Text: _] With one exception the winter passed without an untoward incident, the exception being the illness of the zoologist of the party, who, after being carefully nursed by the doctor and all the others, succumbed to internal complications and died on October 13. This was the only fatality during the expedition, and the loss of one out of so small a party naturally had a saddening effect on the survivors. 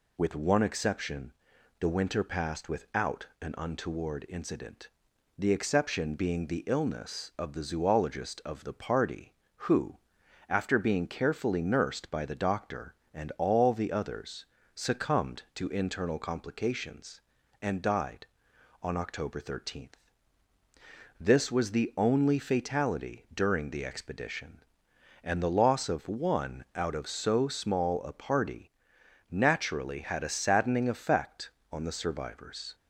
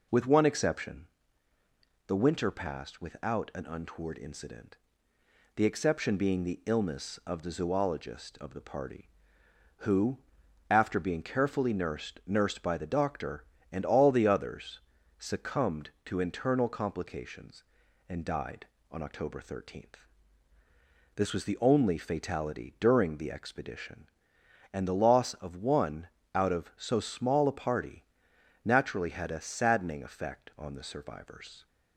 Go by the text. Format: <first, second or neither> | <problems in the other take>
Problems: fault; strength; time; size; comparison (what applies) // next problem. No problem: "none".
first | pauses between "exception" and "the"; at 1.0 s; 1.0 s long; noticeable in the first // says "nursed" twice; at 12.2 s // pauses between "one" and "out"; slight; at 26.0 s; 0.26 s long // pauses between "party" and "naturally"; noticeable; at 28.0 s; 0.58 s long; noticeable in the first